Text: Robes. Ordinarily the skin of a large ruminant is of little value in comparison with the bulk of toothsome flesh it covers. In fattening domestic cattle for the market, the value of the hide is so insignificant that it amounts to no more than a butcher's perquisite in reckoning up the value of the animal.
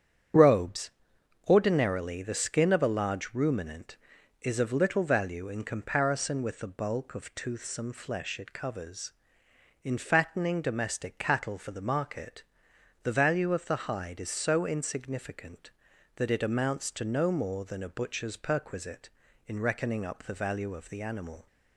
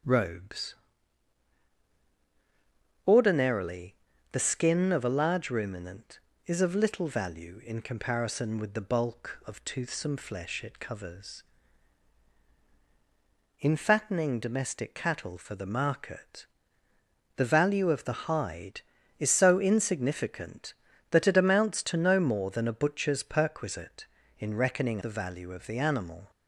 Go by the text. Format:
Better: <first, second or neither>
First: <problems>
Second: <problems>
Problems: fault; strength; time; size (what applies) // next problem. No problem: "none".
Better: first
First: starts louder than the rest; strong; until 1.9 s; 9 dB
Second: starts louder than the rest; strong; until 3.4 s; 8.5 dB // pauses between "Ordinarily" and "the"; at 3.9 s; 0.38 s long // skips "up"; at 25.0 s